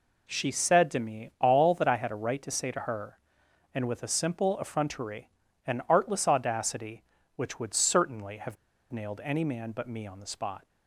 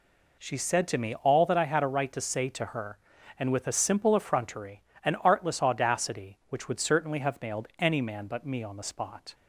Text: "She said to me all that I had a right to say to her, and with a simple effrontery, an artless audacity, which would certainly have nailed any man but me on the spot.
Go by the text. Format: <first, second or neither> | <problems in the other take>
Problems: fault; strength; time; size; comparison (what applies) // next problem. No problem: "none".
second | pauses between "have" and "nailed"; at 8.5 s; 0.37 s long